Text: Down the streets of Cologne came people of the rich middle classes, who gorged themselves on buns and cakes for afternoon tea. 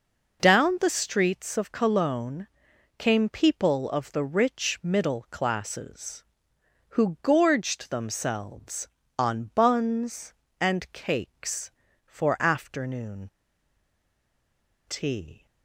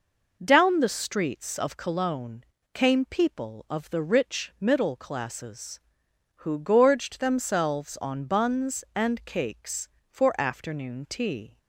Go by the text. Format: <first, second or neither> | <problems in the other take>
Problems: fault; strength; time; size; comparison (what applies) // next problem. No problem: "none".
second | pauses between "Cologne" and "came"; noticeable; at 2.4 s; 0.50 s long; slight in the second // pauses between "afternoon" and "tea"; strong; at 13.2 s; 1.5 s long